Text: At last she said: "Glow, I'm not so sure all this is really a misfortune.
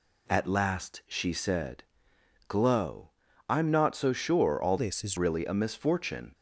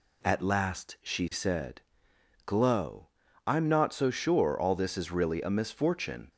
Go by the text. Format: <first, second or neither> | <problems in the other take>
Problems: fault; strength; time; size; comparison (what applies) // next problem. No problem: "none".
second | changes voice from "this" to "is"; from 4.7 to 5.1 s; 0.4 s long